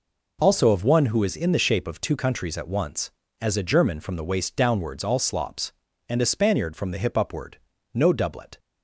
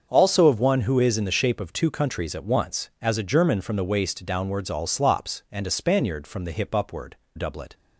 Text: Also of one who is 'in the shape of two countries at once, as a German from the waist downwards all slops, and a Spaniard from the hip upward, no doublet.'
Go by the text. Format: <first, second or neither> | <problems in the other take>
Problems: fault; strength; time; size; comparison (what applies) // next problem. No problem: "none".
first | starts louder than the rest; until 1.1 s; 7 dB // skips "no"; at 7.2 s